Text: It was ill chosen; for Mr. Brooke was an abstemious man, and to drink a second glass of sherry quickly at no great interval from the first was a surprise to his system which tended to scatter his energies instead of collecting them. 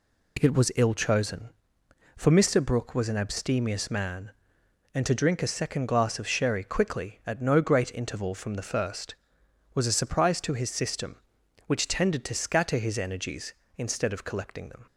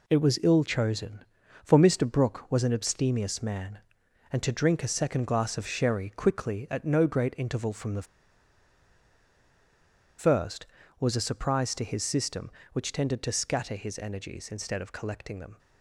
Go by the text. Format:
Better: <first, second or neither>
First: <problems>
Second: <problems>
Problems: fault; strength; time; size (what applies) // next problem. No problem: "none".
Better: first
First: none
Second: pauses between "the" and "first"; strong; at 8.0 s; 2.1 s long